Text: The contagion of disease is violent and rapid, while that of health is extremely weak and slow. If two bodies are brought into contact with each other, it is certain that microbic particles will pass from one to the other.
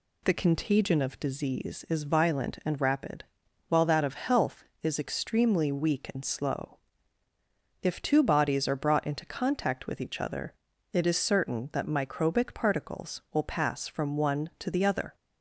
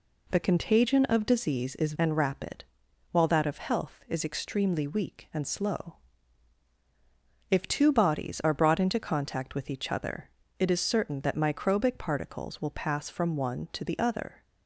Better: first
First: none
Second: skips "violent"; at 1.9 s

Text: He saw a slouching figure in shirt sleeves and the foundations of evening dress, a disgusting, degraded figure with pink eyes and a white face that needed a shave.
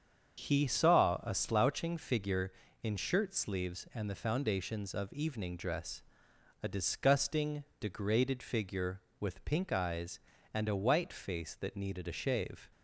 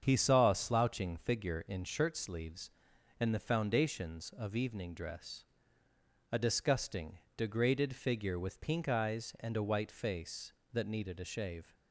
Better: neither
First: starts louder than the rest; strong; until 1.5 s; 7 dB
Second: starts louder than the rest; strong; until 1.0 s; 7.5 dB

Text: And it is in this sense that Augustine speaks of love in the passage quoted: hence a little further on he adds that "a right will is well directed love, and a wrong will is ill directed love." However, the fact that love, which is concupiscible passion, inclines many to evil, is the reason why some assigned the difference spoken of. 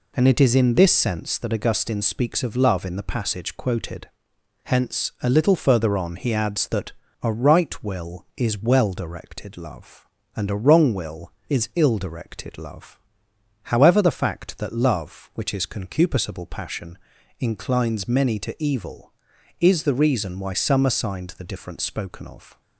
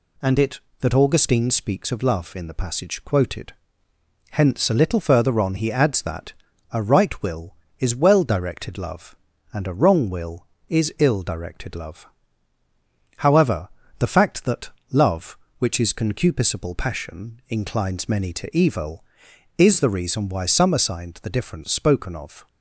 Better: first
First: pauses between "that" and "a"; slight; at 6.9 s; 0.30 s long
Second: skips "is in this sense"; at 0.6 s // pauses between "that" and "a"; at 6.3 s; 0.38 s long // pauses between "that" and "love"; slight; at 14.6 s; 0.22 s long

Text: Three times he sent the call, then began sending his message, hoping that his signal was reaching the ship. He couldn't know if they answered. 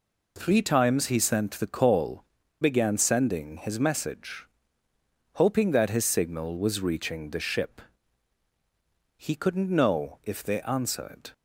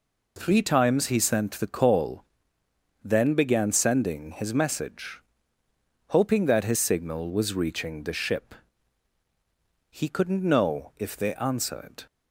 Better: second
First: skips "then"; at 2.4 s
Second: none

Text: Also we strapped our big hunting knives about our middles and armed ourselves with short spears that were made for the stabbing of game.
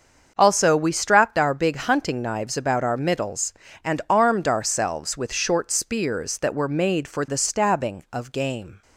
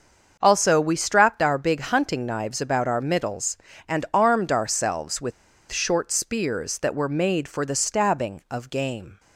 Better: first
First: starts louder than the rest; until 1.3 s; 6.5 dB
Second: starts louder than the rest; until 1.4 s; 6.5 dB // pauses between "with" and "short"; at 5.3 s; 0.39 s long

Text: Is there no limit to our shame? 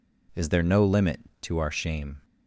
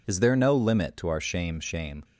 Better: first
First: none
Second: says "shame" twice; at 1.5 s

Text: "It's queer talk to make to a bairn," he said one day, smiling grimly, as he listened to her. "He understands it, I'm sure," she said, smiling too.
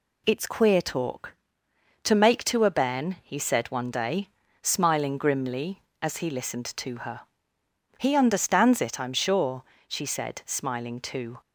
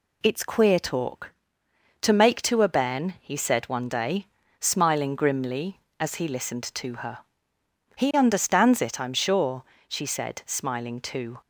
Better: neither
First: none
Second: none

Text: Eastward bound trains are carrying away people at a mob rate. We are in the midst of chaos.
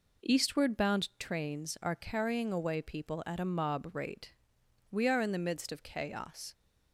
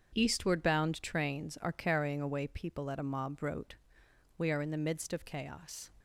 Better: first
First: none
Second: starts louder than the rest; until 1.1 s; 7 dB // says "wrote" for "rate"; at 3.4 s

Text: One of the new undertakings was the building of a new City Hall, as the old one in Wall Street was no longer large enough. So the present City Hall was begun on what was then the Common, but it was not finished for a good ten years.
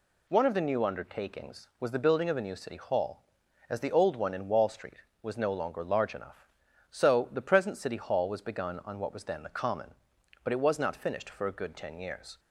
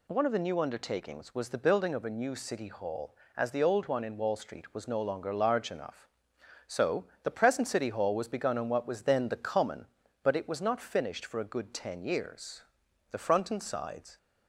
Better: first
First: none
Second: pauses between "So" and "the"; slight; at 7.0 s; 0.20 s long // goes on to say "The front and sides"; noticeable; from 13.1 s on; 1.0 s long

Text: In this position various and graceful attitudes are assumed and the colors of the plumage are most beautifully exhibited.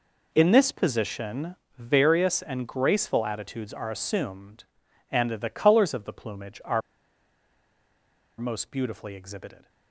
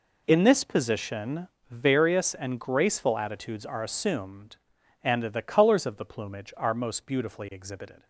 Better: second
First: pauses between "position" and "various"; slight; at 1.5 s; 0.22 s long // pauses between "are" and "most"; strong; at 6.8 s; 1.5 s long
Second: pauses between "position" and "various"; slight; at 1.4 s; 0.22 s long

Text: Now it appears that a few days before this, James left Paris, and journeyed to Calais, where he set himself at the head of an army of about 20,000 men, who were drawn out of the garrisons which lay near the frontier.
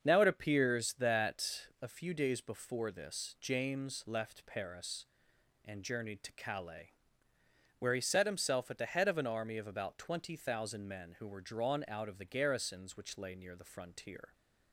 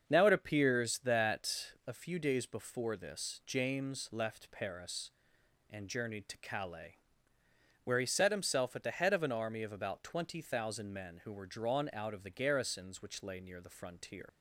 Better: first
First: starts louder than the rest; until 1.0 s; 7 dB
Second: starts louder than the rest; until 1.1 s; 7 dB // leaves "frontier" unfinished; at 14.2 s; 80 ms

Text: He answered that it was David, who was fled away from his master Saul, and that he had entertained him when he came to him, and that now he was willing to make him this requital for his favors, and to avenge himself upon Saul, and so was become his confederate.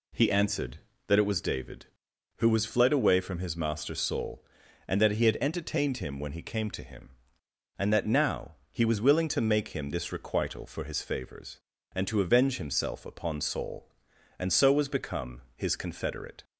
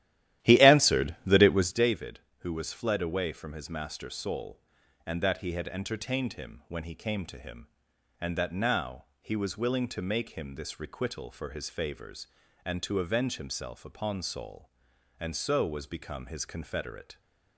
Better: first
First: pauses between "now" and "he"; slight; at 8.5 s; 0.20 s long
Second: starts louder than the rest; strong; until 1.9 s; 13.5 dB // pauses between "now" and "he"; slight; at 9.0 s; 0.16 s long

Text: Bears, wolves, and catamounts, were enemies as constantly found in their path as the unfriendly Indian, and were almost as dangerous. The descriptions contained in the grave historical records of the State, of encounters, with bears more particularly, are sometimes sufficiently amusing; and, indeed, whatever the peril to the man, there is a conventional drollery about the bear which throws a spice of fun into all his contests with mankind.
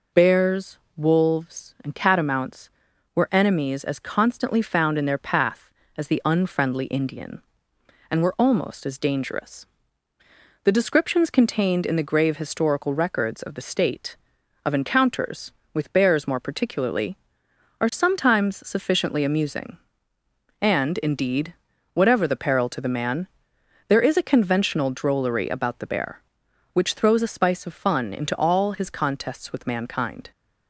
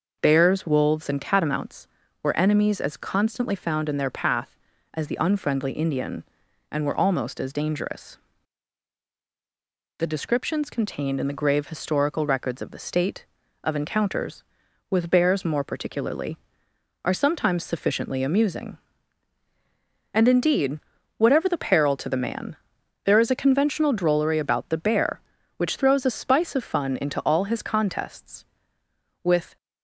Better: first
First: none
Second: stops before "mankind"; at 29.5 s

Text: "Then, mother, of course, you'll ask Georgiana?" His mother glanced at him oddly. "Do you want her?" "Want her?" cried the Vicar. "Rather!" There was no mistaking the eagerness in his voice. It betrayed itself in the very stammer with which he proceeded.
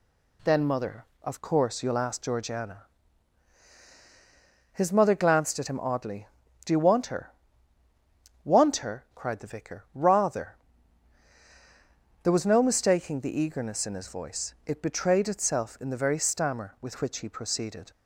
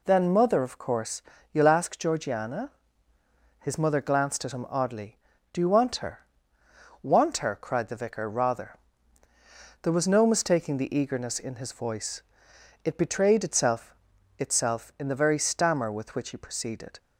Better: first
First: none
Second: says "itself" twice; at 14.3 s

